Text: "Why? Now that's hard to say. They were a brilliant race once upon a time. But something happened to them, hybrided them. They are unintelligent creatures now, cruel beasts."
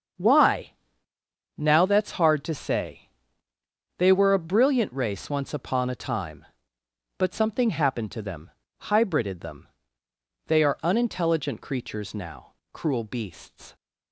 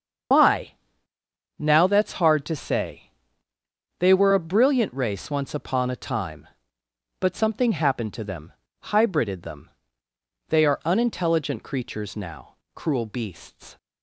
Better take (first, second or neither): first